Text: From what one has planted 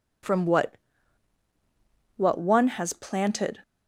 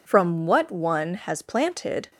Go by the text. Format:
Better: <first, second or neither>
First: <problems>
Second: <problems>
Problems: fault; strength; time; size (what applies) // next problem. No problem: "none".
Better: second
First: says "what" twice; at 2.1 s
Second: none